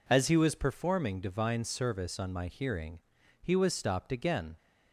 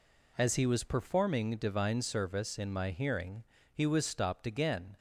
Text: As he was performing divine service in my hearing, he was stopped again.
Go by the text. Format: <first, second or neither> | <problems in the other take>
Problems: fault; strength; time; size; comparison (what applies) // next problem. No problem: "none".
second | says "on" for "in"; at 2.1 s